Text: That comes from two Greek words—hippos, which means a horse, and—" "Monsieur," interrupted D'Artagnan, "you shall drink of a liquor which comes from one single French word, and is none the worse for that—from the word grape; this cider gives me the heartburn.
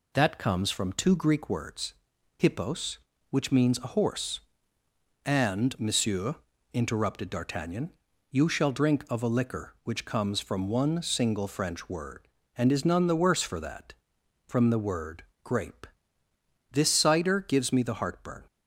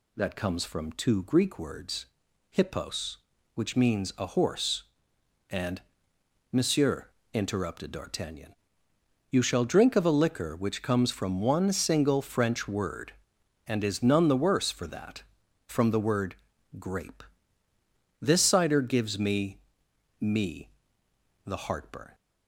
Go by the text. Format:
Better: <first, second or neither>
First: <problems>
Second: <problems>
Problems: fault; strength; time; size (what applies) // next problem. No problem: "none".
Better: first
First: pauses between "word" and "grape"; slight; at 15.2 s; 0.20 s long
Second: pauses between "word" and "grape"; at 16.3 s; 0.42 s long // says "me" twice; at 20.2 s